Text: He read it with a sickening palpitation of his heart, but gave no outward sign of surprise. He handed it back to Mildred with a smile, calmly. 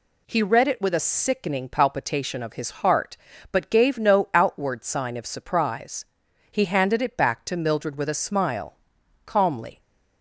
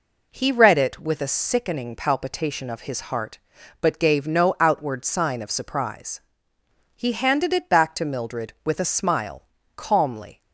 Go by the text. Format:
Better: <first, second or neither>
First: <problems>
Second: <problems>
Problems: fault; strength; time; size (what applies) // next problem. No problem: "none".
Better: neither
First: none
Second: none